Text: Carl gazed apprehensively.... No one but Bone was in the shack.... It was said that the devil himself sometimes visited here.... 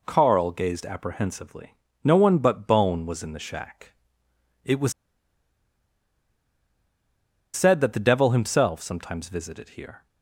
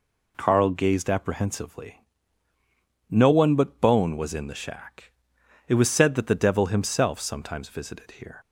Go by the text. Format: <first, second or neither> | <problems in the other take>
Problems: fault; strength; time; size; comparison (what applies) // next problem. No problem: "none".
second | pauses between "was" and "said"; strong; at 4.9 s; 2.6 s long